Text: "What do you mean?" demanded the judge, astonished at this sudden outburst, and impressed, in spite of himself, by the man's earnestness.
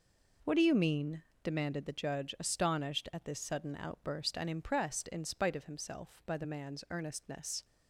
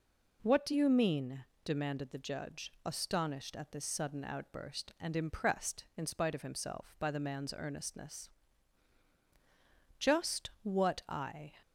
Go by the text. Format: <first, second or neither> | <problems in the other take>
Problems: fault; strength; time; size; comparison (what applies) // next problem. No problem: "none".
first | goes on to say "Just what I"; from 9.9 s on; 1.5 s long